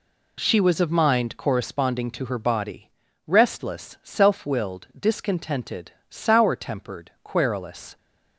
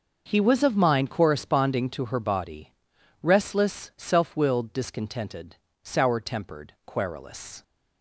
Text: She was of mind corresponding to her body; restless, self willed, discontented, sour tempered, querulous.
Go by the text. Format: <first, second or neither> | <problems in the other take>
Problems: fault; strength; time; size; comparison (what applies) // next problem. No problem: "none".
first | says "He" for "She"; at 0.2 s